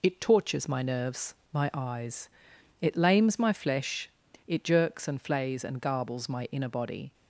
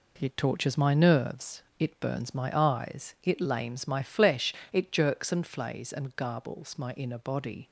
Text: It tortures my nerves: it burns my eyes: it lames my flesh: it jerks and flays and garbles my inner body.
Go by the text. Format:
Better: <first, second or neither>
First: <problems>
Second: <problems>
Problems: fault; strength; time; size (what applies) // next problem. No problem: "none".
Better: second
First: skips "it burns"; at 1.4 s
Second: none